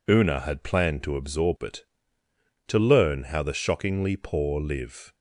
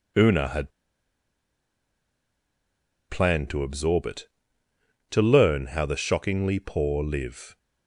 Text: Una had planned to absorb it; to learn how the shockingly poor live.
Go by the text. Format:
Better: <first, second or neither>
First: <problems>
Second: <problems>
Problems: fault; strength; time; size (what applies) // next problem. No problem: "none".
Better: first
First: none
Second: pauses between "had" and "planned"; strong; at 0.7 s; 2.3 s long